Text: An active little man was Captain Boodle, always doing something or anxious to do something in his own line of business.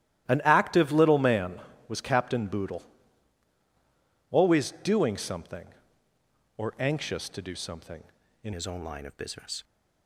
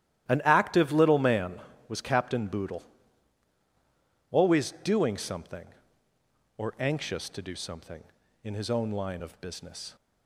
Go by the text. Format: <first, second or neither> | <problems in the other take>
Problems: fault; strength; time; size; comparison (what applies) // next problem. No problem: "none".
second | starts louder than the rest; strong; until 1.3 s; 13.5 dB; strong in the second // changes voice at "his"; from 8.5 s on; 1.1 s long